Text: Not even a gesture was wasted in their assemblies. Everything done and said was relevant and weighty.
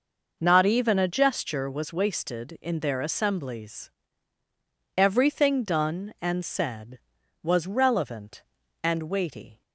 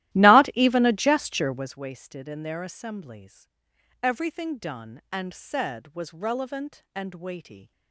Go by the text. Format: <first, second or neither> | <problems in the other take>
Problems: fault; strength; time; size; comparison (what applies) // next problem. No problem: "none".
first | starts louder than the rest; strong; until 1.8 s; 15 dB